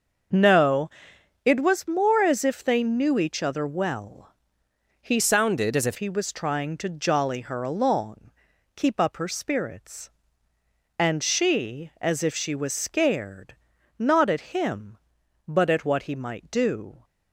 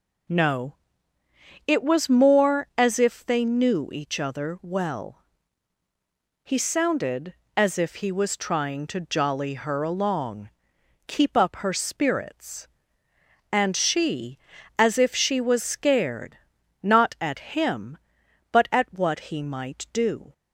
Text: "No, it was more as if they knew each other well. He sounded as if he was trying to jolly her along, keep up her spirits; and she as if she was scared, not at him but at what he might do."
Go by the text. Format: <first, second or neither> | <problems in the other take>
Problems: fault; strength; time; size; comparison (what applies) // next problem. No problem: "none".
second | starts louder than the rest; until 1.8 s; 6.5 dB // changes voice from "sounded" to "if"; from 5.1 to 5.9 s; 0.8 s long